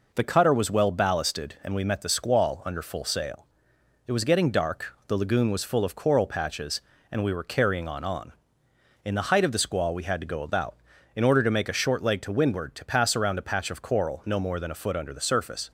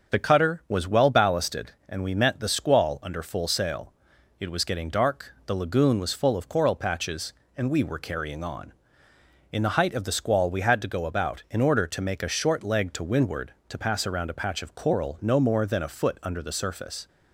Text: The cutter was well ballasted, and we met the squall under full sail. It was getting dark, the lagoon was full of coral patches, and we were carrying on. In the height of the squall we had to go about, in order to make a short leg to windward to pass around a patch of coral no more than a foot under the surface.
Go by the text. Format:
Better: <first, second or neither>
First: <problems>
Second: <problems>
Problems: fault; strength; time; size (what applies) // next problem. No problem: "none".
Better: second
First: says "on" twice; at 8.0 s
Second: none